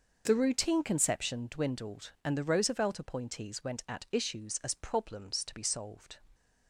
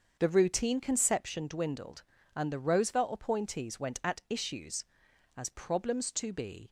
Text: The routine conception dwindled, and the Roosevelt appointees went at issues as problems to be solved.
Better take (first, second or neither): first